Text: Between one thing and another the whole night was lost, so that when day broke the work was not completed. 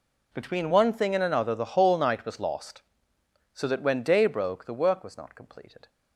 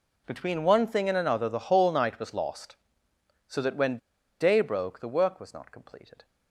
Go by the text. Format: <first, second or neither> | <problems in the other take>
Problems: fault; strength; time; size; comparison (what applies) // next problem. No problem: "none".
first | pauses between "when" and "day"; at 3.9 s; 0.42 s long